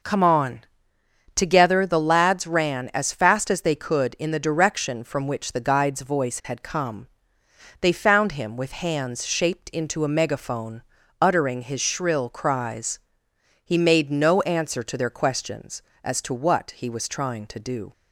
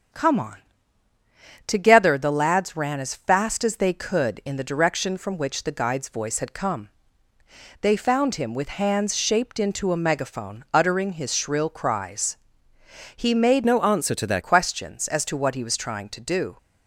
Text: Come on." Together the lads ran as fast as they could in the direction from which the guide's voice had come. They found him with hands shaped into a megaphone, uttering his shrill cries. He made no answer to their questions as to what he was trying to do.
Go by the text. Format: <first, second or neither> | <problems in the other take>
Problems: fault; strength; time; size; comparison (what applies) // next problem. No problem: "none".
first | starts louder than the rest; strong; until 2.2 s; 7.5 dB // changes voice from "no" to "their"; from 13.6 to 14.4 s; 0.8 s long